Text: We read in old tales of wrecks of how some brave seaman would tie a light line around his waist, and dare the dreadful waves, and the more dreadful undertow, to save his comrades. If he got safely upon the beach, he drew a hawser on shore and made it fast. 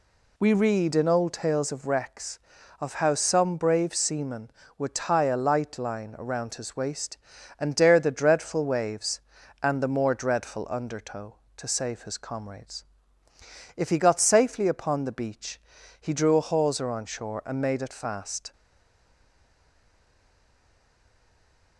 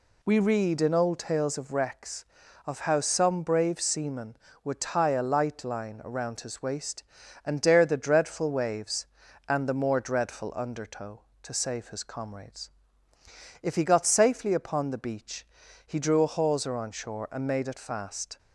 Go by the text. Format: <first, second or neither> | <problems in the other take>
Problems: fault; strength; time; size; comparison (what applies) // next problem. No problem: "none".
second | stays silent after the last word; strong; from 18.5 s on; 3.2 s long